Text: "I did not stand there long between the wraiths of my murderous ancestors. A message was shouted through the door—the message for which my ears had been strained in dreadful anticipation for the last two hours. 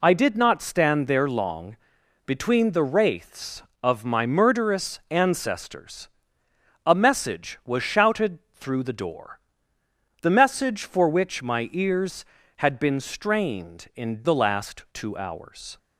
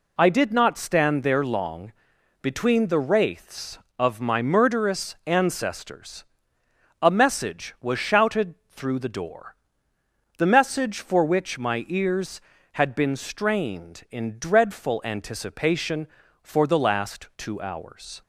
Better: second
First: pauses between "long" and "between"; noticeable; at 1.7 s; 0.48 s long // pauses between "shouted" and "through"; slight; at 8.3 s; 0.16 s long // skips "dreadful anticipation for"; at 14.2 s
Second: pauses between "long" and "between"; noticeable; at 1.9 s; 0.48 s long // pauses between "shouted" and "through"; slight; at 8.5 s; 0.16 s long

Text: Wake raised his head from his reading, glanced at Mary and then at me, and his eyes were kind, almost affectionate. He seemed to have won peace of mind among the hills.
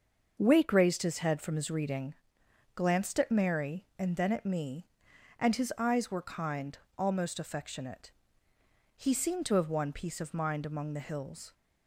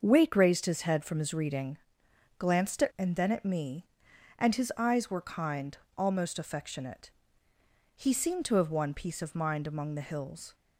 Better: first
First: starts louder than the rest; until 1.3 s; 6.5 dB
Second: starts louder than the rest; until 1.0 s; 6.5 dB // skips "Mary"; at 2.9 s

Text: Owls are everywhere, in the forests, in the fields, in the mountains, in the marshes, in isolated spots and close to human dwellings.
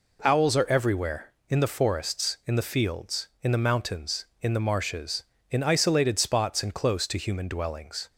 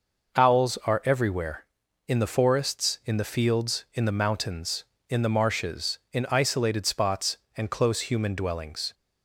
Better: first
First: none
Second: skips "to"; at 8.0 s

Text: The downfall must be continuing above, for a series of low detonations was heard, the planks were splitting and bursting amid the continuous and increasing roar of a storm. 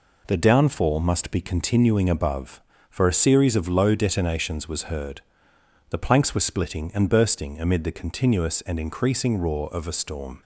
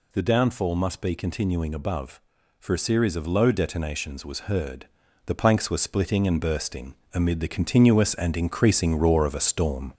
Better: first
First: none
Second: gets louder; throughout; 3.5 dB // pauses between "bursting" and "amid"; slight; at 6.9 s; 0.18 s long

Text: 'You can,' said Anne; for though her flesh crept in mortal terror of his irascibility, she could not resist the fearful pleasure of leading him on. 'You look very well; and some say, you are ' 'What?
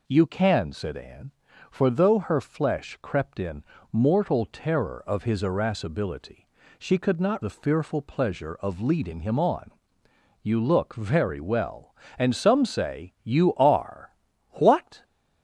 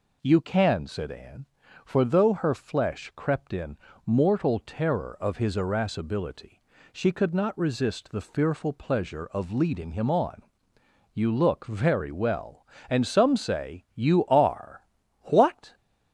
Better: second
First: pauses between "in" and "mortal"; slight; at 3.6 s; 0.28 s long // skips "resist"; at 7.4 s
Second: pauses between "in" and "mortal"; slight; at 3.7 s; 0.28 s long

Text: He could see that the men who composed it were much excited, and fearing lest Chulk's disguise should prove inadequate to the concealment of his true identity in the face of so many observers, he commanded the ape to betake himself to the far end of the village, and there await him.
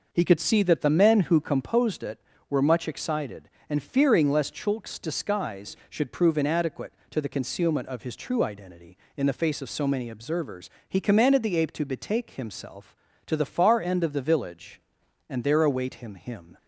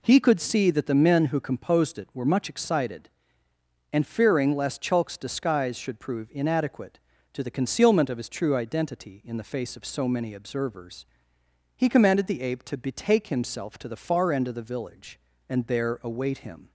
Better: second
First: says "him" twice; at 16.1 s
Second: none

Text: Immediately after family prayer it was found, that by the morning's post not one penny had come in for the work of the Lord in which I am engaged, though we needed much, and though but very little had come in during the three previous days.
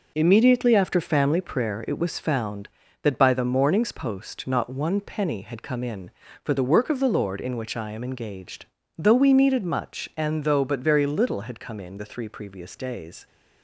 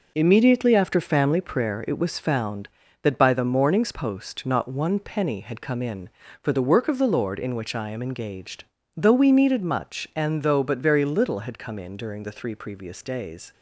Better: second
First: skips "during"; at 11.9 s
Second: none

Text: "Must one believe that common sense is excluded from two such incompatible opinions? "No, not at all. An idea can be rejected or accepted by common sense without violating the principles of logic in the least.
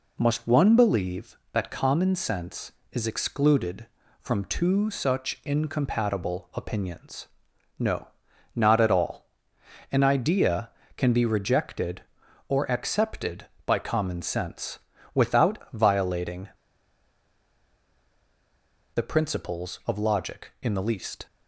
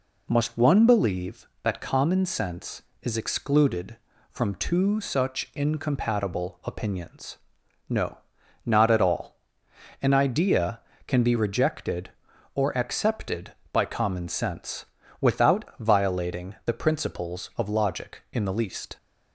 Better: second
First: pauses between "sense" and "without"; slight; at 14.8 s; 0.34 s long // pauses between "violating" and "the"; strong; at 16.4 s; 2.4 s long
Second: pauses between "sense" and "without"; slight; at 14.8 s; 0.34 s long

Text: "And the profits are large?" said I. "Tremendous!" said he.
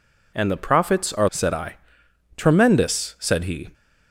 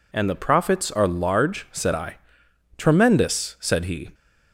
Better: second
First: skips "large"; at 1.2 s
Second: none

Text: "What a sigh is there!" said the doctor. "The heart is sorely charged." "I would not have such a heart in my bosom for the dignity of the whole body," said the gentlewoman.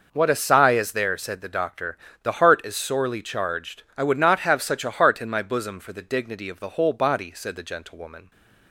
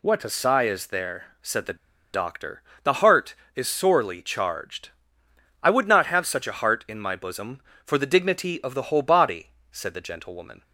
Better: first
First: none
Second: pauses between "the" and "doctor"; at 1.7 s; 0.37 s long

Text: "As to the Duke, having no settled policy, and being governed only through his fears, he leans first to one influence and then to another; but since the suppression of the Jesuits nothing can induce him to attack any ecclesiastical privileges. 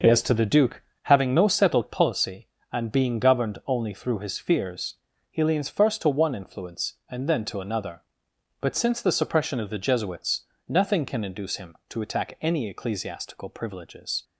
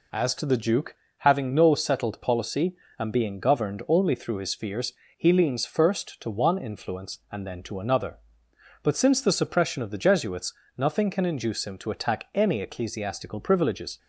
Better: neither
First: pauses between "Jesuits" and "nothing"; slight; at 10.4 s; 0.26 s long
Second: pauses between "Jesuits" and "nothing"; slight; at 10.5 s; 0.24 s long

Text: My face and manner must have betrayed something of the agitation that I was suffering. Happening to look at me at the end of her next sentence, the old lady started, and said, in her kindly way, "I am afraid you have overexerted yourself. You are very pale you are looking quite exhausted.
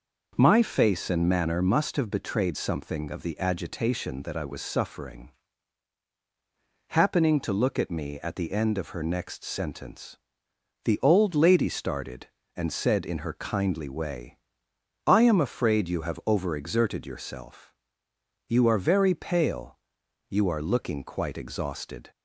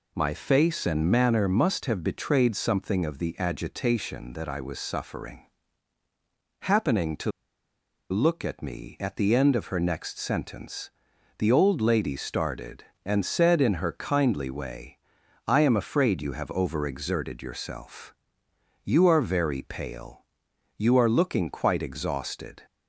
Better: first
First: pauses between "pale" and "you"; noticeable; at 19.7 s; 0.56 s long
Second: pauses between "to" and "look"; noticeable; at 7.3 s; 0.79 s long // pauses between "pale" and "you"; noticeable; at 20.1 s; 0.60 s long

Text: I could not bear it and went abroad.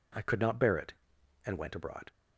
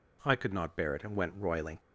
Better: first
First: none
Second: says "roiling" for "abroad"; at 1.3 s

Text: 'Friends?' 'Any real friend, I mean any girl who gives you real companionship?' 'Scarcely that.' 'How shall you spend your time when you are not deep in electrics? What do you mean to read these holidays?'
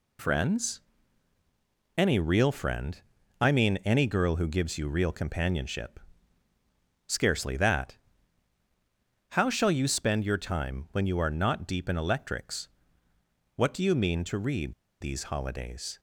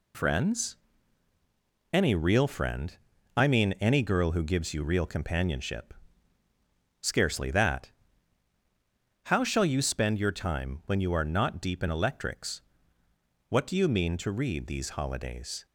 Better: second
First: pauses between "read" and "these"; slight; at 14.7 s; 0.27 s long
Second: none

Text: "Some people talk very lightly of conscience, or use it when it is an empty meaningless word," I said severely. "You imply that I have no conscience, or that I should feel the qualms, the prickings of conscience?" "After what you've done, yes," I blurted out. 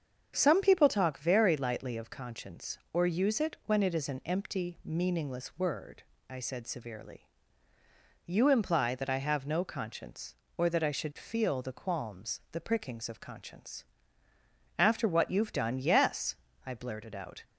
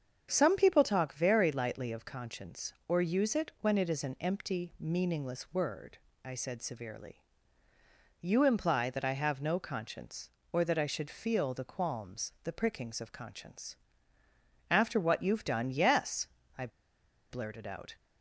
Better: first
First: starts louder than the rest; strong; until 1.3 s; 7.5 dB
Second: starts louder than the rest; strong; until 1.3 s; 7.5 dB // pauses between "I" and "blurted"; noticeable; at 16.6 s; 0.62 s long

